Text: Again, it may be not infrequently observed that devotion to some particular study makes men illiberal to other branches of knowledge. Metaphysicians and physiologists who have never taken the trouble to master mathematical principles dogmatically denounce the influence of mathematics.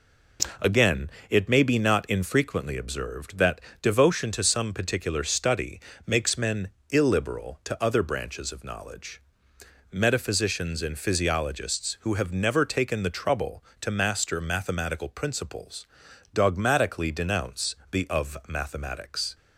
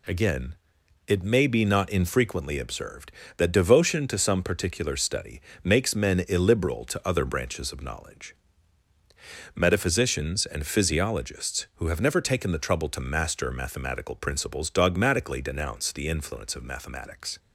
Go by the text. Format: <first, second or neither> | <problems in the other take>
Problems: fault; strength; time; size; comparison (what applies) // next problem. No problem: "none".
second | pauses between "that" and "devotion"; slight; at 3.6 s; 0.20 s long // pauses between "study" and "makes"; slight; at 5.7 s; 0.28 s long; slight in the second // pauses between "men" and "illiberal"; slight; at 6.6 s; 0.22 s long // pauses between "principles" and "dogmatically"; noticeable; at 15.8 s; 0.48 s long // pauses between "denounce" and "the"; slight; at 17.7 s; 0.16 s long // skips "influence"; at 18.0 s